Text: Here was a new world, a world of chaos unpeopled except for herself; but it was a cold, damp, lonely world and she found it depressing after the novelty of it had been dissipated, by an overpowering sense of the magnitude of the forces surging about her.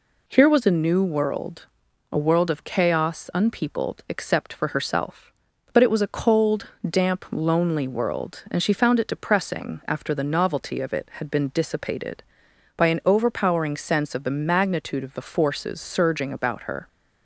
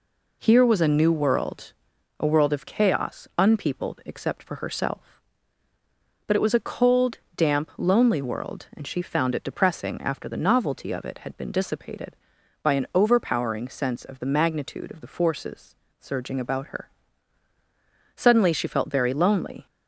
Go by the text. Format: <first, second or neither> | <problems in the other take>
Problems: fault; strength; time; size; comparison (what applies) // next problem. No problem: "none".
first | pauses between "forces" and "surging"; slight; at 15.7 s; 0.24 s long // goes on to say "Suddenly she felt very lonely"; from 18.1 s on; 1.5 s long